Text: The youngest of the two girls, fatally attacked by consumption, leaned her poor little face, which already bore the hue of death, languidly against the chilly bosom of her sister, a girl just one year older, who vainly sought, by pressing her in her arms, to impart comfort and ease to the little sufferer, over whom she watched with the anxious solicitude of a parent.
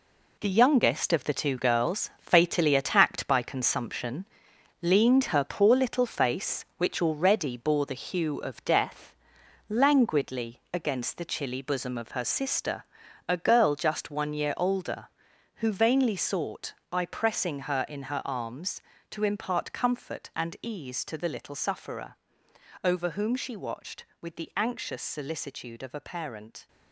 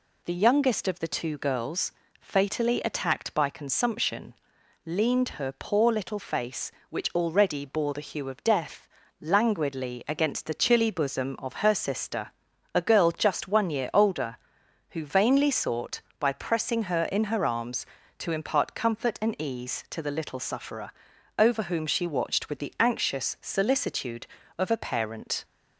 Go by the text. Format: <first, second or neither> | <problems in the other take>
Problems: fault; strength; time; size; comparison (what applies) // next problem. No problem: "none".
second | gets quieter; strong; throughout; 8.5 dB